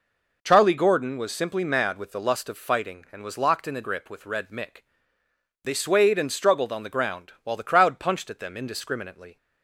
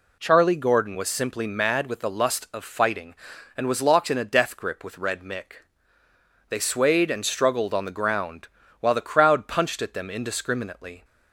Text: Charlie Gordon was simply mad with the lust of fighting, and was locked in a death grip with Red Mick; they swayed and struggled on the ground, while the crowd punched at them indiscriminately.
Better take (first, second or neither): second